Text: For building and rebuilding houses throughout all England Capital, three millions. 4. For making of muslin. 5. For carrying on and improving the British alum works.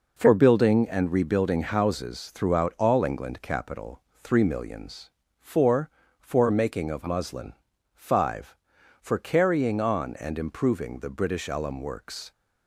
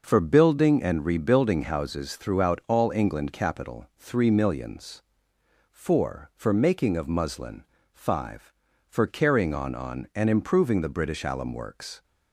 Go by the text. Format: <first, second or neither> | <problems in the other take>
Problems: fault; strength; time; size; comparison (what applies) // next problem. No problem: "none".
first | says "on" twice; at 9.7 s